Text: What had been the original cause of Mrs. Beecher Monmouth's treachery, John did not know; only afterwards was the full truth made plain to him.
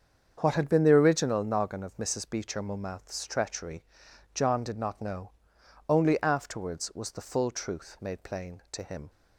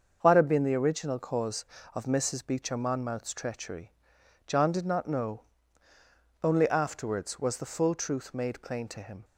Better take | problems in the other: second | starts louder than the rest; strong; until 1.4 s; 7.5 dB; also in the second // says "noggin" for "cause"; at 1.4 s

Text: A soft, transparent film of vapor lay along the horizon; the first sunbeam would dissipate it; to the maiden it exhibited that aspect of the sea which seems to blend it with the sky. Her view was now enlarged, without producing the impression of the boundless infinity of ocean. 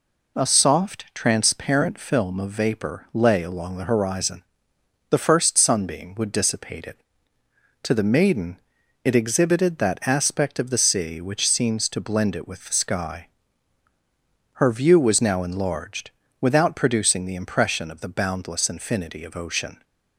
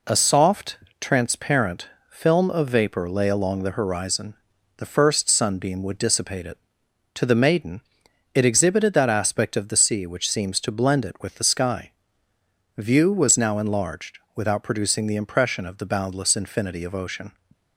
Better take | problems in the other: first | pauses between "transparent" and "film"; slight; at 1.8 s; 0.22 s long // pauses between "maiden" and "it"; noticeable; at 7.7 s; 0.54 s long; noticeable in the first // skips "Her"; at 12.3 s

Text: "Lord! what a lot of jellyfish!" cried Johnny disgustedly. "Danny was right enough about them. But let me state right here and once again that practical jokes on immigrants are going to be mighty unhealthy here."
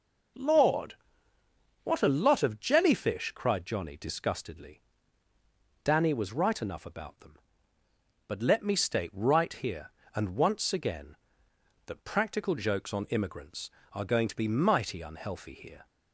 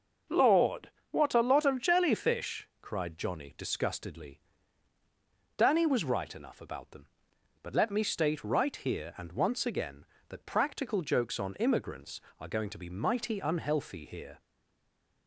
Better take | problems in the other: first | starts louder than the rest; noticeable; until 1.5 s; 6 dB // stays silent after the last word; slight; from 14.3 s on; 0.9 s long

